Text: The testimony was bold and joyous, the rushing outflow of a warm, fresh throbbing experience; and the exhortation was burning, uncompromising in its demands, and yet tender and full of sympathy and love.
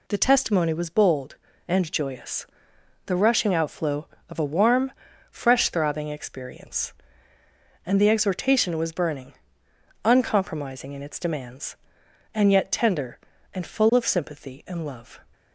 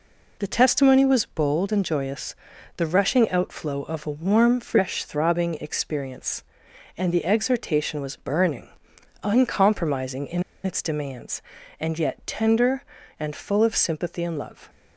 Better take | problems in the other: first | pauses between "in" and "its"; slight; at 10.4 s; 0.22 s long

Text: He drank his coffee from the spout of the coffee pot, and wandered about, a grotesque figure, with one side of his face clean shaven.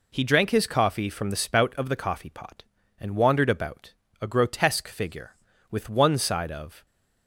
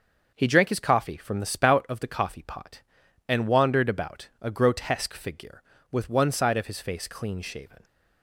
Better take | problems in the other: second | stops before "his face clean shaven"; at 6.8 s

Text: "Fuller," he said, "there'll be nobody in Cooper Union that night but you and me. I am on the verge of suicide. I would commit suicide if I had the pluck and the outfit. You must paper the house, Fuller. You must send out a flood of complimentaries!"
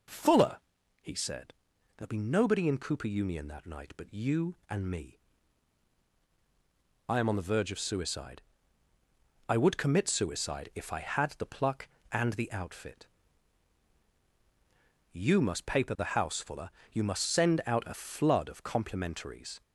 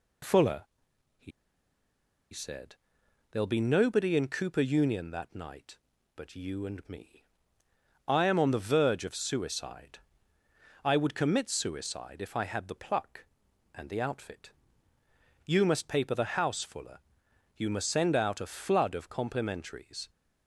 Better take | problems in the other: first | pauses between "he" and "said"; at 1.3 s; 1.0 s long

